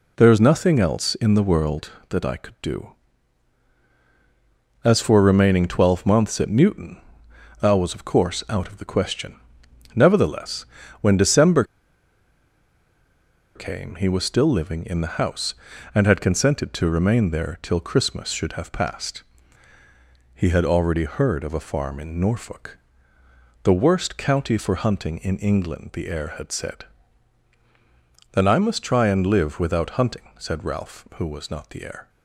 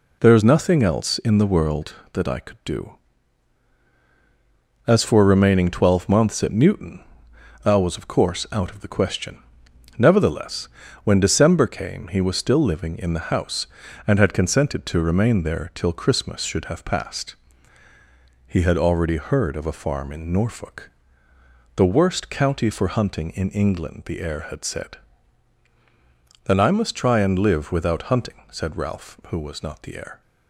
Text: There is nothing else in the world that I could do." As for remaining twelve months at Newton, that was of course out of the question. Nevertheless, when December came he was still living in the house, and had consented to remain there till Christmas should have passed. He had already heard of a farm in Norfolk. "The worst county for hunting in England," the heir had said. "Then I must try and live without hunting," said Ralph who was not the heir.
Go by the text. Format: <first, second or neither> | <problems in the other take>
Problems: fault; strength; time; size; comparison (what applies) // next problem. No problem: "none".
second | pauses between "December" and "came"; strong; at 11.6 s; 1.9 s long